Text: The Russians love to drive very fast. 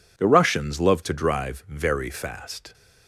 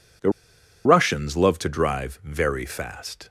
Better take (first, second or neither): first